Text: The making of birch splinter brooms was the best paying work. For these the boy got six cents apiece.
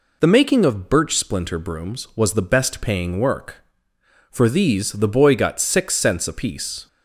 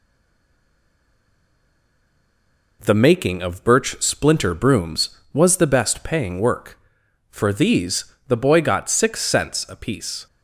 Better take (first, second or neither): first